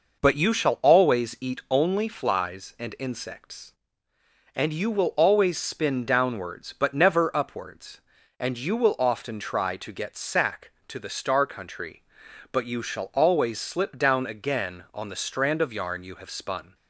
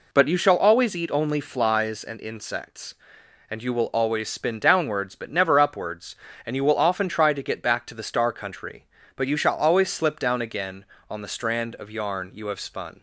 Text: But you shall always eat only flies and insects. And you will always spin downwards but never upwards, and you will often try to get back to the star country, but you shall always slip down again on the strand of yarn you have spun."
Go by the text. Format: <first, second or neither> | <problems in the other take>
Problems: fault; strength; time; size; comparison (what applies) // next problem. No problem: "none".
second | says "sack" for "back"; at 10.1 s